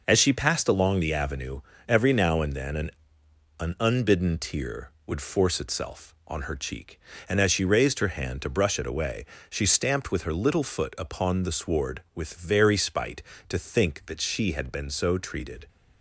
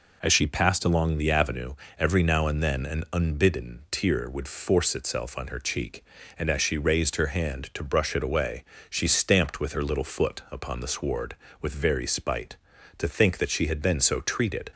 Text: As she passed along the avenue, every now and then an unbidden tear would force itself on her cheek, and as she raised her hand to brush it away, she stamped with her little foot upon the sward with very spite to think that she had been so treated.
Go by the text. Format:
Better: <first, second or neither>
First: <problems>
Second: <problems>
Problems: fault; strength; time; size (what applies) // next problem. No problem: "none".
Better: second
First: says "an" twice; at 3.5 s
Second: none